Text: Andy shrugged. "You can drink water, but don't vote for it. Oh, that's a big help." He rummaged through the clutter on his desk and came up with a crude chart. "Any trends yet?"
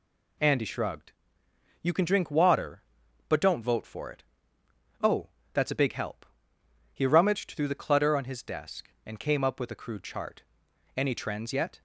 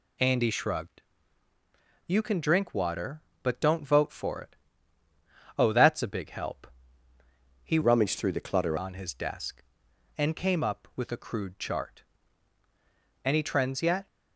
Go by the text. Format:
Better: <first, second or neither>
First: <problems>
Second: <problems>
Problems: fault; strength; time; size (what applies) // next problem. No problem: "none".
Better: first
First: none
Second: changes voice from "rummaged" to "clutter"; from 7.8 to 8.7 s; 0.9 s long